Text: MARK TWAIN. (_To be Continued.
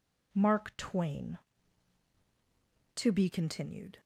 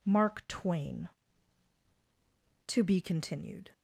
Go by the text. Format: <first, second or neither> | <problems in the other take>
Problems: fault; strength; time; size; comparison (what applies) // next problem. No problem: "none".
neither | none